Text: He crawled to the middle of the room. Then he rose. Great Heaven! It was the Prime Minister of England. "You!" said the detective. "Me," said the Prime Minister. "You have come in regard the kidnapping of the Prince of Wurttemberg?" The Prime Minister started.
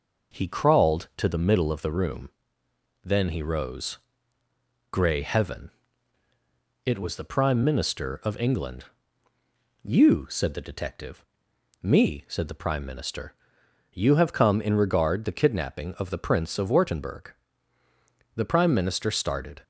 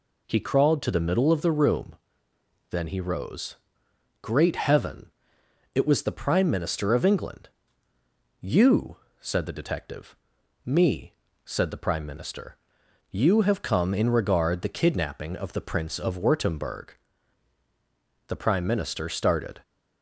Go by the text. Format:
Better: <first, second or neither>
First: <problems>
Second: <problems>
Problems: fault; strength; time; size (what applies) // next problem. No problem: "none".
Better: second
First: says "Grey" for "Great"; at 4.9 s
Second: none